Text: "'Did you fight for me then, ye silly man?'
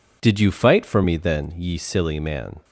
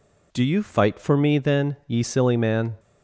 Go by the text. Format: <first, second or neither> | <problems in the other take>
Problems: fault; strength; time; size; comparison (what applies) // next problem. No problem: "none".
first | says "Do" for "Did"; at 0.3 s